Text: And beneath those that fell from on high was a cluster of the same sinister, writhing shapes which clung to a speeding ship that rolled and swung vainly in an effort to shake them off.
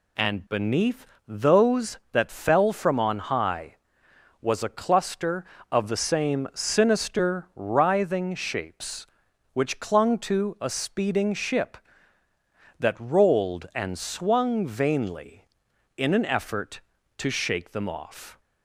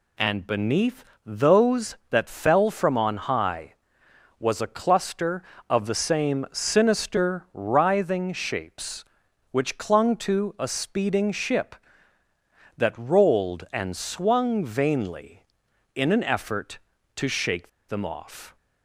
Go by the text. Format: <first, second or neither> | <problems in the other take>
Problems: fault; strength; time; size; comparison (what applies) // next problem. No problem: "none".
first | pauses between "beneath" and "those"; slight; at 1.0 s; 0.20 s long; slight in the first // pauses between "shake" and "them"; slight; at 17.6 s; 0.18 s long